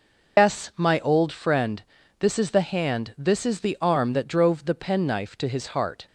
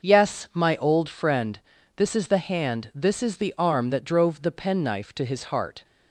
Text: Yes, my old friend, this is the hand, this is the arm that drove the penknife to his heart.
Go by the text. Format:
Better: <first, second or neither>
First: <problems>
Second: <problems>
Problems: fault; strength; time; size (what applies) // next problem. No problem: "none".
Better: second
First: loses the start of "Yes"; at 0.3 s; 105 ms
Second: none